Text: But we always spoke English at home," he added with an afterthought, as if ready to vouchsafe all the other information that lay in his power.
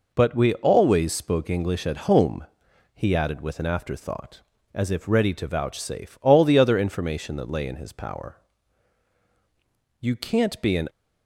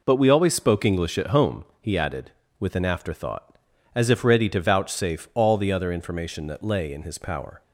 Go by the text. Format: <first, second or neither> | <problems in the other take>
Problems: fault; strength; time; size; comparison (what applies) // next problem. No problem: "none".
second | goes on to say "You can't be an"; noticeable; from 10.0 s on; 0.88 s long